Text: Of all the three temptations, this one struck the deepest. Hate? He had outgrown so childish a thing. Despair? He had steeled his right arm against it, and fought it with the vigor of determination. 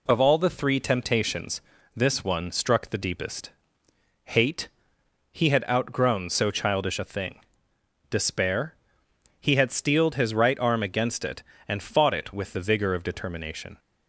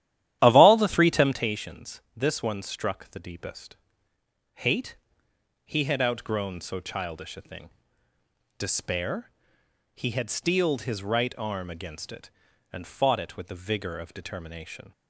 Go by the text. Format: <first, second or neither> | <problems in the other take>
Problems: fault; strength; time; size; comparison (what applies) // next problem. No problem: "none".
first | starts louder than the rest; strong; until 1.5 s; 12 dB